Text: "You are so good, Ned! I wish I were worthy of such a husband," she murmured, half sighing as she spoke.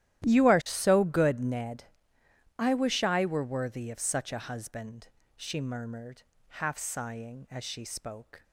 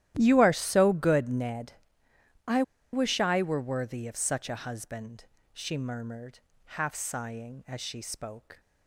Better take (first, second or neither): first